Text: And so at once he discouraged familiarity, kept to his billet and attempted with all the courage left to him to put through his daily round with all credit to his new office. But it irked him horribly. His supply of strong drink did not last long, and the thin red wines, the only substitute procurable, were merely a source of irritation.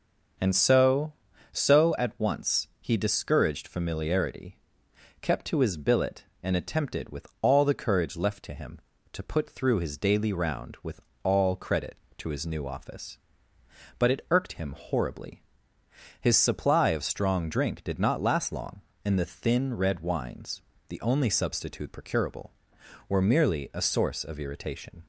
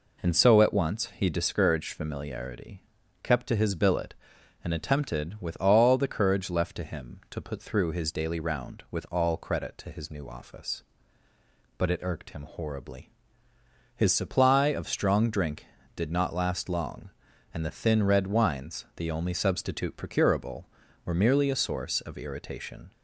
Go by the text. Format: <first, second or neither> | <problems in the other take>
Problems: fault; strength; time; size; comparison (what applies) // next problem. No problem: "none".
second | starts louder than the rest; noticeable; until 1.7 s; 6 dB // says "so" twice; at 1.5 s // pauses between "with" and "all"; slight; at 10.9 s; 0.24 s long